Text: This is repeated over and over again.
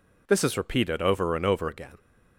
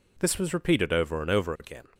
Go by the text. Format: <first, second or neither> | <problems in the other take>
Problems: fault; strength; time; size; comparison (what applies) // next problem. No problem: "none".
first | says "was" for "is"; at 0.3 s